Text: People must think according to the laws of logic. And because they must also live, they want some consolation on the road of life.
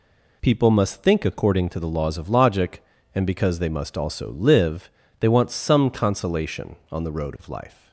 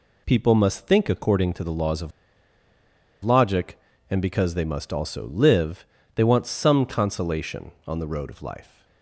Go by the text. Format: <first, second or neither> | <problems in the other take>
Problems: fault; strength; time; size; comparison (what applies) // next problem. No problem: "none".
first | pauses between "of" and "logic"; at 2.1 s; 1.1 s long